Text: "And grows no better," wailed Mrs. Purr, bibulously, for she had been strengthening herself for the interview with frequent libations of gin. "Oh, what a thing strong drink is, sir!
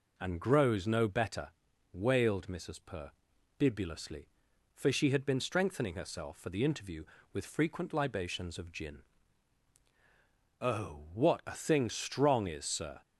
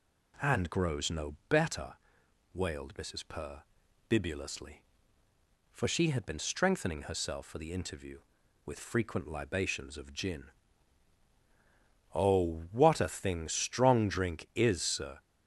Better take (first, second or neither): second